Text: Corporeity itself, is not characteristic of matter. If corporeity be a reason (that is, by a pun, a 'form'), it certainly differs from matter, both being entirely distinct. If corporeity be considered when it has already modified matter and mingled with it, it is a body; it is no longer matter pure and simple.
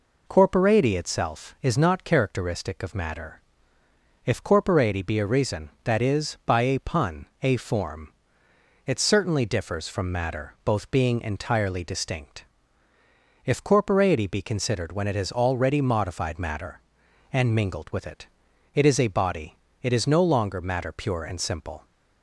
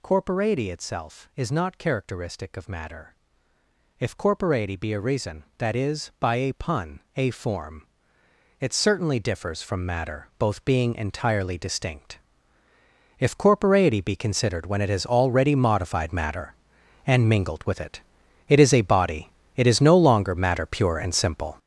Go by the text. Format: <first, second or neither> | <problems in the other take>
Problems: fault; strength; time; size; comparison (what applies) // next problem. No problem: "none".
first | gets louder; strong; throughout; 9.5 dB